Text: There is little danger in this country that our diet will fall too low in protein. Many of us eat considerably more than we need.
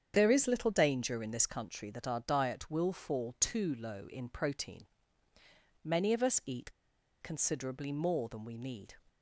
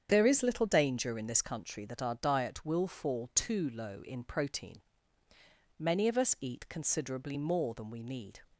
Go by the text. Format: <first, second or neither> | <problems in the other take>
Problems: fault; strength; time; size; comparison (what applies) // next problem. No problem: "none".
second | starts louder than the rest; strong; until 1.1 s; 8 dB; strong in the second // pauses between "eat" and "considerably"; noticeable; at 6.7 s; 0.49 s long